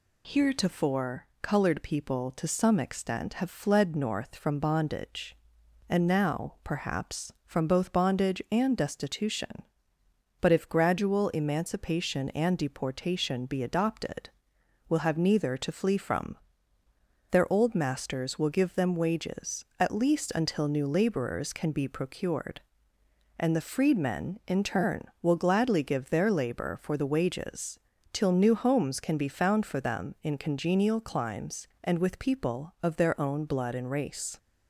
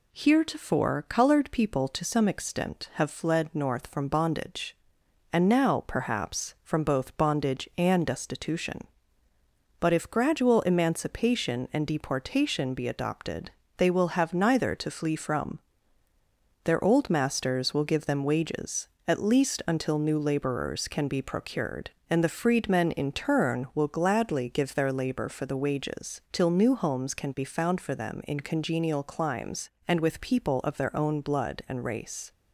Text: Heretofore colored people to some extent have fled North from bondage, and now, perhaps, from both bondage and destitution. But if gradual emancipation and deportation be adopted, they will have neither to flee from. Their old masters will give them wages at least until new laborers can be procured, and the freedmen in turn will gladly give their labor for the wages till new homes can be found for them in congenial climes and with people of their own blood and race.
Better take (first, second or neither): second